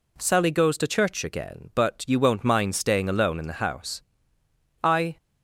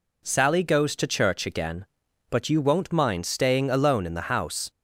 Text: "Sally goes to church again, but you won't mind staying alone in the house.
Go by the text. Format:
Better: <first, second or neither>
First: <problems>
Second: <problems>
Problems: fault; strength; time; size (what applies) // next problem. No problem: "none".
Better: second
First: goes on to say "I"; slight; from 4.8 s on; 0.34 s long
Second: none